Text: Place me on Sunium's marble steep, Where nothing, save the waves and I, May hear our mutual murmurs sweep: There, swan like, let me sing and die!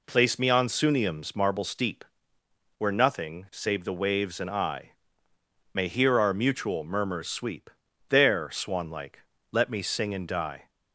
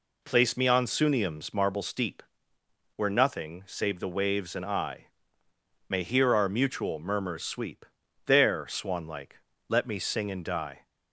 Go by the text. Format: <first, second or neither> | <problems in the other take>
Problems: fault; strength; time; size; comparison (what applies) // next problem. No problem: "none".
neither | none